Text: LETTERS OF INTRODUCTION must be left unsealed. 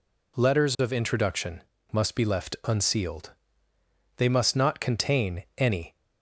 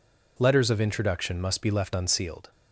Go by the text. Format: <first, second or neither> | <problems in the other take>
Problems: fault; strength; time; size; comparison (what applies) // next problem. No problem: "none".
second | pauses between "INTRODUCTION" and "must"; slight; at 1.6 s; 0.32 s long // goes on to say "They must not contain any"; strong; from 4.1 s on; 1.7 s long